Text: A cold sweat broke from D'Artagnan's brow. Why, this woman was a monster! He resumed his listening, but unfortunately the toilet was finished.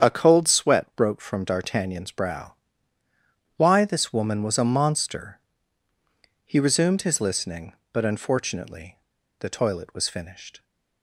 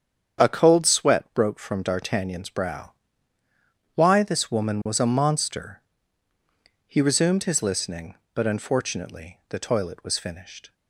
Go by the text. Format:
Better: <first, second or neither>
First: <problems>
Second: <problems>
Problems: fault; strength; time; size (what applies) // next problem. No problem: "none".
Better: second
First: starts louder than the rest; strong; until 1.1 s; 8 dB // pauses between "unfortunately" and "the"; at 8.9 s; 0.42 s long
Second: starts louder than the rest; strong; until 1.5 s; 8 dB